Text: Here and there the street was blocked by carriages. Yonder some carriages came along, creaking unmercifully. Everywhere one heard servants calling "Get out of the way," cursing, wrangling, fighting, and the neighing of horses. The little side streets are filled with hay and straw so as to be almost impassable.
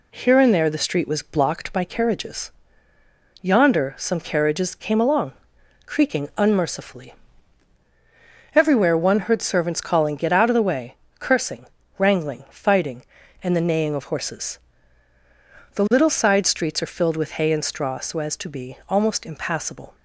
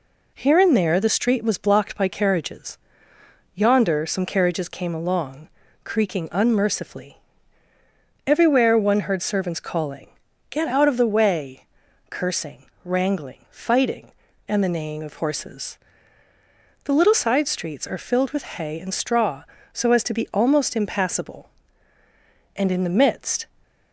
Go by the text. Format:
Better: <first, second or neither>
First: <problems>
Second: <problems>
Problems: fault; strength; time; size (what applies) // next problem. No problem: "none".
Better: first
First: none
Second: pauses between "calling" and "Get"; at 10.0 s; 0.40 s long // goes on to say "And in the midst"; noticeable; from 22.5 s on; 0.90 s long